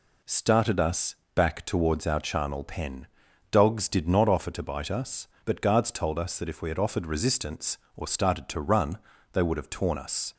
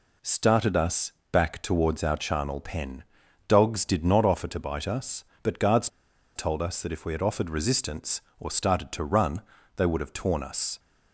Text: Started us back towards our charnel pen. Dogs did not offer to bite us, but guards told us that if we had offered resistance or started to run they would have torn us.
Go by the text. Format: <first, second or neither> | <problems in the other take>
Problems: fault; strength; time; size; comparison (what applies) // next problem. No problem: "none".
first | pauses between "us" and "back"; slight; at 1.1 s; 0.18 s long; slight in the first // pauses between "guards" and "told"; noticeable; at 5.8 s; 0.48 s long // pauses between "run" and "they"; slight; at 9.4 s; 0.34 s long; slight in the first